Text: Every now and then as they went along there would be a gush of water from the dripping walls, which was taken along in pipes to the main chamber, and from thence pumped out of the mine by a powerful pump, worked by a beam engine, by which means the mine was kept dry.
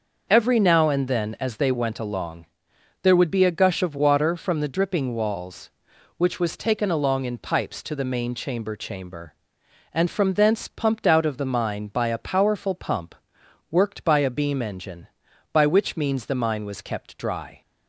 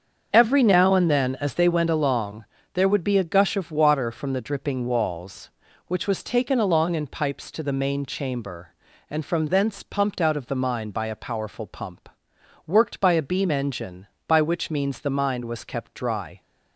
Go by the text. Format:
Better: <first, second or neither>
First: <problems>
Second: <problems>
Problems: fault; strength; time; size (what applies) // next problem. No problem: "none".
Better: second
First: starts louder than the rest; noticeable; until 1.3 s; 6 dB // pauses between "along" and "there"; noticeable; at 2.4 s; 0.56 s long // says "chamber" twice; at 8.7 s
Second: starts louder than the rest; until 1.3 s; 7 dB // pauses between "along" and "there"; slight; at 2.4 s; 0.28 s long